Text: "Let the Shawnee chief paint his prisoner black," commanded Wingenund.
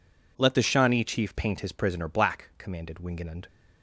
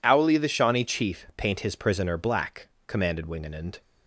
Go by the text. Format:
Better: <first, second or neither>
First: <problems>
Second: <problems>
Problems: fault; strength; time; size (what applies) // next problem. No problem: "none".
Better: first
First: none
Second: says "Owly" for "Let"; at 0.0 s